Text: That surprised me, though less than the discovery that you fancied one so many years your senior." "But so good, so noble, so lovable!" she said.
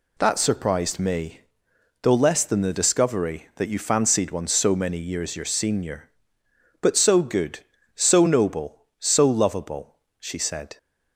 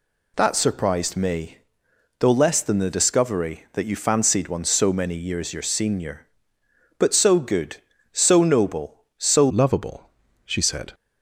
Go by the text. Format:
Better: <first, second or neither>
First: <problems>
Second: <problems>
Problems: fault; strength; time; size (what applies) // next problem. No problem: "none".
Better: first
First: none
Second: changes voice at "lovable"; from 9.5 s on; 1.4 s long